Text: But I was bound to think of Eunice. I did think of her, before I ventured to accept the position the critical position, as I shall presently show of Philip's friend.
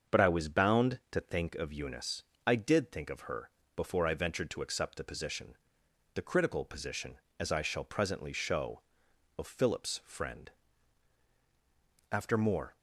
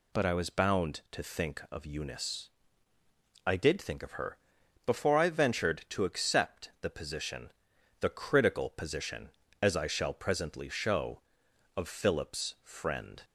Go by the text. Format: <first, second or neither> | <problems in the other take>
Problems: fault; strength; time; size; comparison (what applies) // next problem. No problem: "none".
second | starts louder than the rest; until 1.2 s; 7 dB // pauses between "position" and "the"; noticeable; at 5.5 s; 0.58 s long; noticeable in the second // goes on to say "After more"; noticeable; from 12.0 s on; 0.68 s long